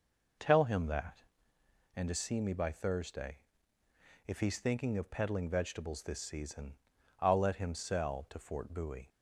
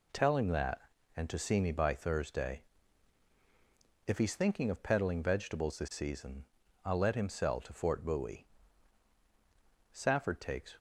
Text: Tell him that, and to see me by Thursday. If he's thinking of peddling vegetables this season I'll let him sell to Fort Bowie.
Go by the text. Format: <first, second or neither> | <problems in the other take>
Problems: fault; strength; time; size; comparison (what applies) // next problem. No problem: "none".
first | pauses between "season" and "I'll"; at 6.4 s; 0.40 s long; noticeable in the first // goes on to say "Safford takes"; noticeable; from 9.9 s on; 0.82 s long